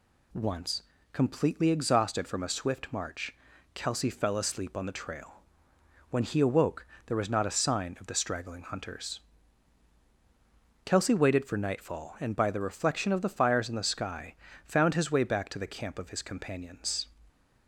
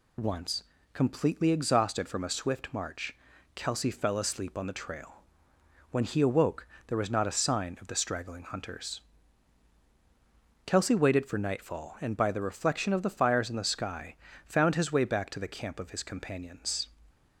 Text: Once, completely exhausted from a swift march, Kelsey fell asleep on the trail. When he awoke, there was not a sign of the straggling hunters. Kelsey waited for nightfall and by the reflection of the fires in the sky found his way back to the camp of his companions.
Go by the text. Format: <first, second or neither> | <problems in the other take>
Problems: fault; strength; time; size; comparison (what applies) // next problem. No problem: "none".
first | loses the start of "Once"; at 0.1 s; 55 ms // pauses between "sky" and "found"; slight; at 14.1 s; 0.32 s long; slight in the first